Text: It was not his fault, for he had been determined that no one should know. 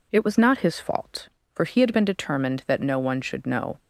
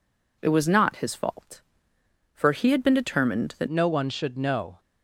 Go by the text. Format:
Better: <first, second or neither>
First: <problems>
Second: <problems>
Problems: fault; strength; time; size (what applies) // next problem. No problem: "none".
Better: first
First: none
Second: changes voice at "no"; from 3.6 s on; 1.1 s long